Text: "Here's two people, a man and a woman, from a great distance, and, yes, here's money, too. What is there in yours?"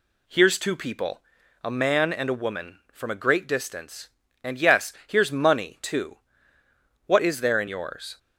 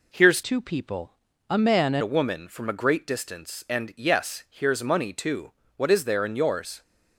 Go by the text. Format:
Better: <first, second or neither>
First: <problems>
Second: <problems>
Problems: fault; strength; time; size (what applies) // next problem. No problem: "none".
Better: first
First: none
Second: changes voice from "two" to "and"; from 0.4 to 2.0 s; 1.6 s long